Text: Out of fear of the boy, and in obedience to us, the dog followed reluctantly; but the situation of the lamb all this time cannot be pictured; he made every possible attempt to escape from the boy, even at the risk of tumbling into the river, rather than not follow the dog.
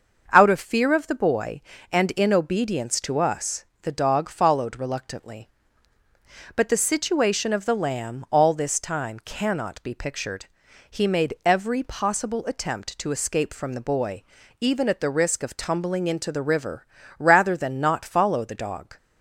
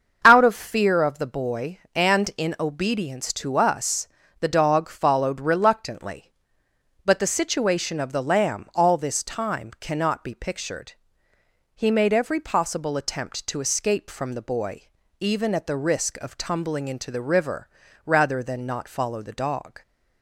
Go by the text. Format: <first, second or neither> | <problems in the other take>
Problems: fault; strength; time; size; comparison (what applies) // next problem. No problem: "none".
neither | starts louder than the rest; the same in both